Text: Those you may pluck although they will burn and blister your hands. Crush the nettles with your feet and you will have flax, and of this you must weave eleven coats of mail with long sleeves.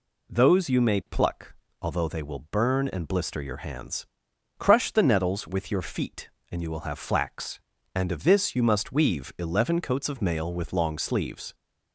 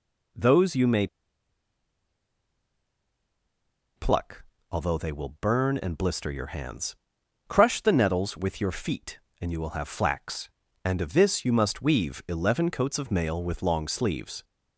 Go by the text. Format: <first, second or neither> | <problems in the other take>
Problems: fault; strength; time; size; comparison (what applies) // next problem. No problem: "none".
first | pauses between "may" and "pluck"; strong; at 1.0 s; 2.8 s long // pauses between "pluck" and "although"; slight; at 4.4 s; 0.30 s long; slight in the first